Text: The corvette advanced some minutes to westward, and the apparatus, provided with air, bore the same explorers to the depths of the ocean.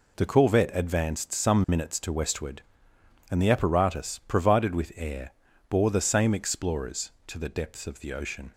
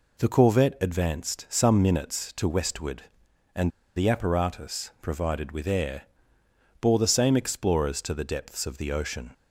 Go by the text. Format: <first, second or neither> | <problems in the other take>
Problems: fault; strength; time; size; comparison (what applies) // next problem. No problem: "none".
first | pauses between "and" and "the"; slight; at 3.6 s; 0.26 s long